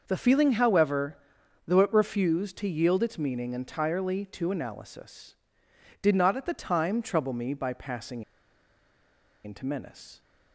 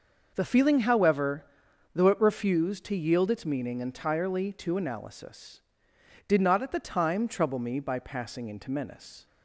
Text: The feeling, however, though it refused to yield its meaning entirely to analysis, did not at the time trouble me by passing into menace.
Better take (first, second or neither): second